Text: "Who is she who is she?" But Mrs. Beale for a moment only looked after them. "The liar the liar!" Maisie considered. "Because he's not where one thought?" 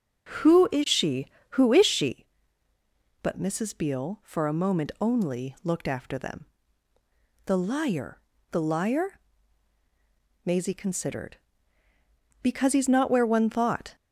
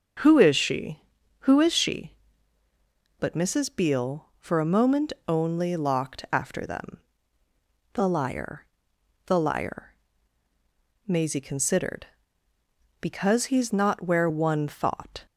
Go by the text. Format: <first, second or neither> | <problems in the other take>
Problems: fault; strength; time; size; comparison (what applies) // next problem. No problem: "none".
first | starts louder than the rest; until 1.6 s; 6.5 dB; also in the first // pauses between "moment" and "only"; slight; at 5.1 s; 0.16 s long // says "locked" for "looked"; at 5.7 s // pauses between "liar" and "the"; noticeable; at 8.6 s; 0.60 s long; slight in the first